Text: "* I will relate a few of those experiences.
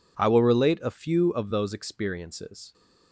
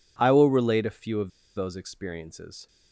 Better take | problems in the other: first | pauses between "of" and "those"; slight; at 1.2 s; 0.27 s long

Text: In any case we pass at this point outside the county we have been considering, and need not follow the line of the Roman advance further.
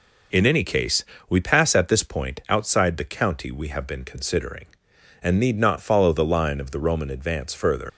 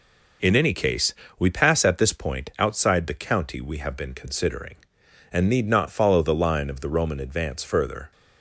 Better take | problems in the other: second | pauses between "case" and "we"; slight; at 1.0 s; 0.24 s long; slight in the second // leaves "further" unfinished; at 7.8 s; 115 ms

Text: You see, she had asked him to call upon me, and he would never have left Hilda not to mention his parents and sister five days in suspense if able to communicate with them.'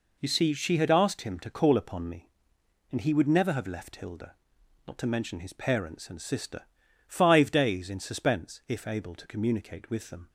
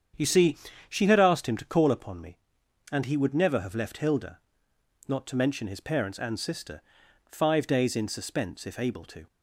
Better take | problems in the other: first | starts louder than the rest; strong; until 1.4 s; 8 dB // pauses between "Hilda" and "not"; noticeable; at 4.3 s; 0.68 s long; noticeable in the first // pauses between "sister" and "five"; noticeable; at 6.8 s; 0.46 s long; noticeable in the first // stops before "communicate with them"; at 9.2 s

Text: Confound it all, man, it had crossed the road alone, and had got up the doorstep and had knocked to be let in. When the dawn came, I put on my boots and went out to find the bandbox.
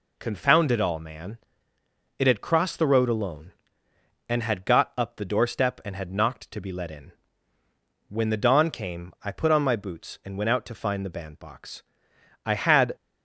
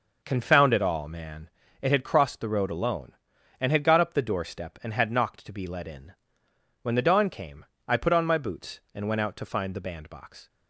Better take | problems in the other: second | goes on to say "I had"; from 12.4 s on; 0.50 s long

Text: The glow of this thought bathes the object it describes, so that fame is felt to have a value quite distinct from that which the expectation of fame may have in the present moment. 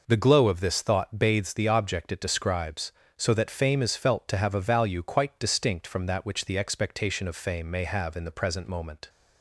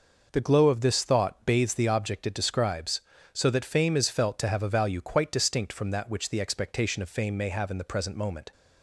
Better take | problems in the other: neither | none

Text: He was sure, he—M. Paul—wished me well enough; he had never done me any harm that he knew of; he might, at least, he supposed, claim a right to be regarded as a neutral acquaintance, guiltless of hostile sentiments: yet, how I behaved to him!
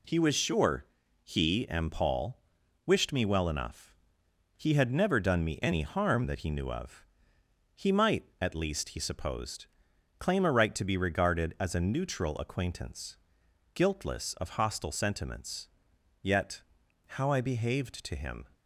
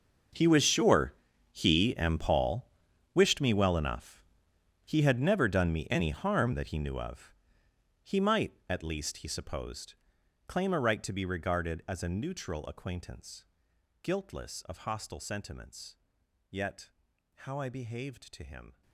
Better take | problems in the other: first | gets quieter; strong; throughout; 17.5 dB

